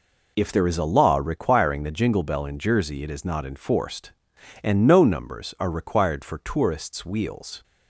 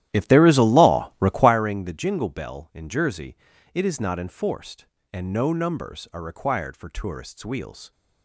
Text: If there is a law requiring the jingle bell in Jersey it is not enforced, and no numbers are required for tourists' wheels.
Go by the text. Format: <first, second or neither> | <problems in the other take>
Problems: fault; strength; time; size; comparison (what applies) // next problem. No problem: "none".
first | starts louder than the rest; strong; until 1.6 s; 13 dB // pauses between "Jersey" and "it"; at 3.3 s; 0.38 s long